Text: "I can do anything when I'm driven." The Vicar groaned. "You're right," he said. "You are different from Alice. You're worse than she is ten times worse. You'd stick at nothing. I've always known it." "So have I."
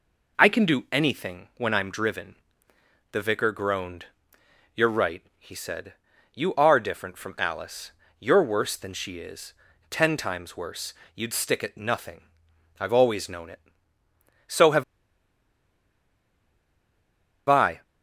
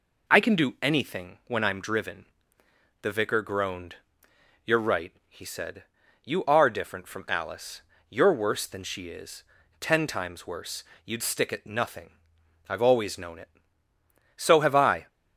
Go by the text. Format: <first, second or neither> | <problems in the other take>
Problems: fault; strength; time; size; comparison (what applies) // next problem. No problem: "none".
second | pauses between "is" and "ten"; at 9.5 s; 0.38 s long; also in the second // pauses between "have" and "I"; strong; at 14.8 s; 2.6 s long